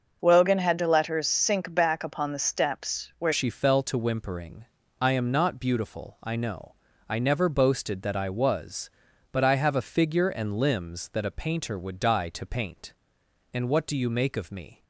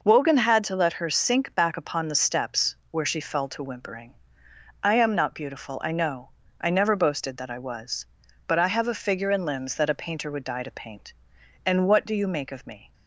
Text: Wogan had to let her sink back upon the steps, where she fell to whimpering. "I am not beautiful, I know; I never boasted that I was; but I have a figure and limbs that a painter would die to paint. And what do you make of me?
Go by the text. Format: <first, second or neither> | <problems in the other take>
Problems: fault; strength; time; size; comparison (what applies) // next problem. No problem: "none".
second | starts louder than the rest; until 1.2 s; 6.5 dB // changes voice at "she"; from 3.3 s on; 11.5 s long